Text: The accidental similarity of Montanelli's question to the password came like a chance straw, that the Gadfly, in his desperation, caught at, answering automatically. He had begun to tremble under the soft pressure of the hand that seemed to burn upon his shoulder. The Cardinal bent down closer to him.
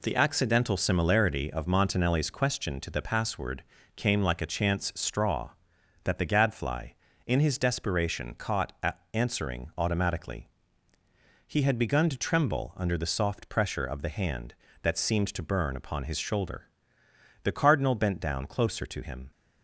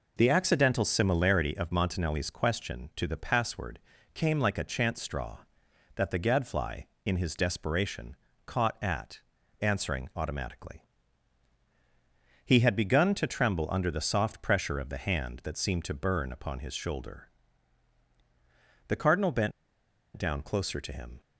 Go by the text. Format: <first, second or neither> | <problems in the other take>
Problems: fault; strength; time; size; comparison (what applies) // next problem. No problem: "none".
first | pauses between "password" and "came"; at 3.7 s; 0.38 s long; slight in the first // pauses between "bent" and "down"; noticeable; at 19.5 s; 0.64 s long